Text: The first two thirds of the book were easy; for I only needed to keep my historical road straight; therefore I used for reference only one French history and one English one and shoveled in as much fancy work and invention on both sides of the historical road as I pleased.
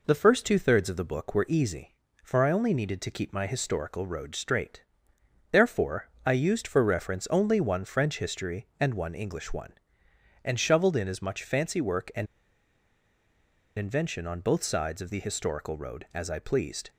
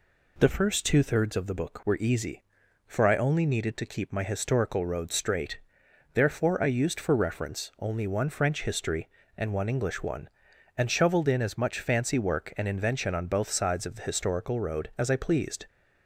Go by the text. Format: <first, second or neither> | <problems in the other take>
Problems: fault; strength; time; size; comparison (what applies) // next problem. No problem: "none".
second | pauses between "therefore" and "I"; slight; at 6.1 s; 0.16 s long // pauses between "and" and "invention"; strong; at 12.2 s; 1.5 s long